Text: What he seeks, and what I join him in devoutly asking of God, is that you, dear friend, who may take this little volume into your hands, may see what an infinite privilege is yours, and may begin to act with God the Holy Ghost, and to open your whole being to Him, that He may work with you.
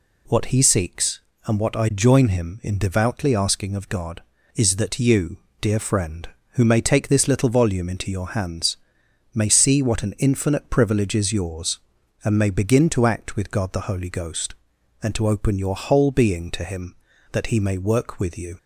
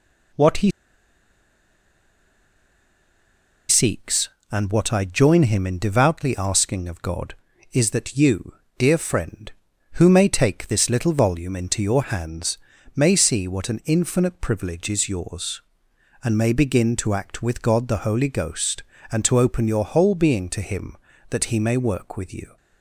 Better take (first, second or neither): first